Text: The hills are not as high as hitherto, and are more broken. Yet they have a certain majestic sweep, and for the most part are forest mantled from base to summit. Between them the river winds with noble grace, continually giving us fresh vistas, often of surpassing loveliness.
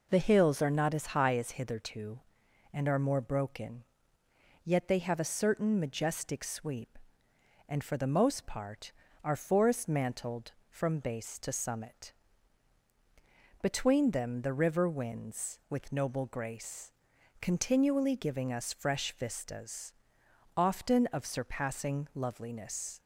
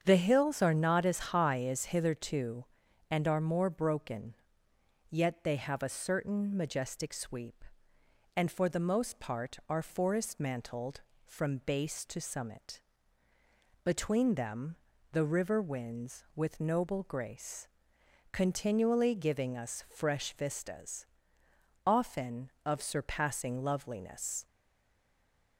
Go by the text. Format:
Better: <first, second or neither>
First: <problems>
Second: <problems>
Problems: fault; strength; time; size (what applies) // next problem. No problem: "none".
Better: first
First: none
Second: starts louder than the rest; strong; until 1.0 s; 7.5 dB // pauses between "them" and "the"; at 14.7 s; 0.38 s long // stays silent after the last word; from 24.4 s on; 1.1 s long